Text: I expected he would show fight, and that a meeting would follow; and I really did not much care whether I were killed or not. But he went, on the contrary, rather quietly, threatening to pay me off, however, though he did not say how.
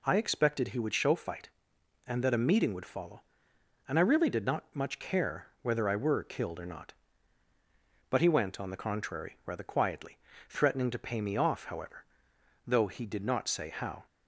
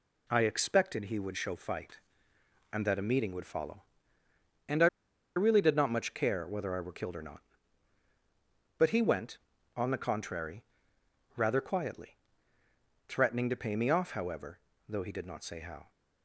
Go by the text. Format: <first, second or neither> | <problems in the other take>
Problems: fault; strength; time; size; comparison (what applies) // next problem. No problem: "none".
first | pauses between "I" and "really"; noticeable; at 4.8 s; 0.49 s long